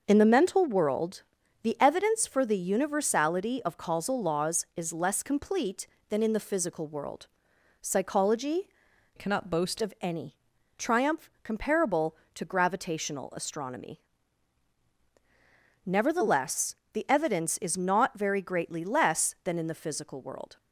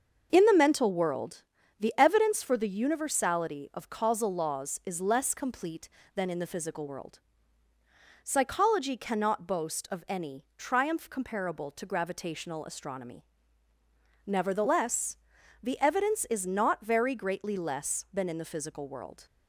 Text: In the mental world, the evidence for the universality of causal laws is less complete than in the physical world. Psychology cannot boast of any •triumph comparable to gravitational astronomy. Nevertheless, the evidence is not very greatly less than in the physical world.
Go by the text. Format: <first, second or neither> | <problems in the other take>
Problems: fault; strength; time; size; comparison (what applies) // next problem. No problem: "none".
second | starts louder than the rest; until 1.0 s; 6 dB; also in the second // changes voice from "cannot" to "boast"; from 9.1 to 9.7 s; 0.6 s long